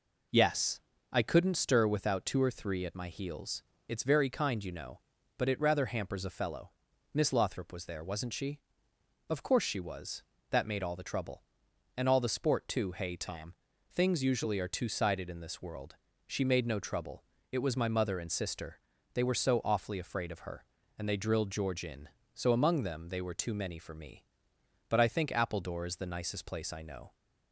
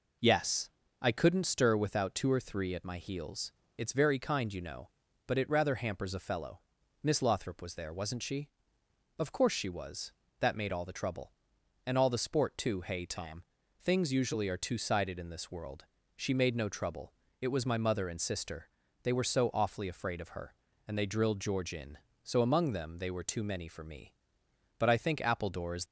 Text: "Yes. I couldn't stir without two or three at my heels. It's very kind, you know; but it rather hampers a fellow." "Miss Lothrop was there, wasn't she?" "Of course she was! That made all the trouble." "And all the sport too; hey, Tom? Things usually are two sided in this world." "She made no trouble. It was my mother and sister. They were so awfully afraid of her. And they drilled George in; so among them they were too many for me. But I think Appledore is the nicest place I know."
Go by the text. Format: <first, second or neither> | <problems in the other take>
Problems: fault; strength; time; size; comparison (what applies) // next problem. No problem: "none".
first | stops before "the nicest place I know"; at 25.8 s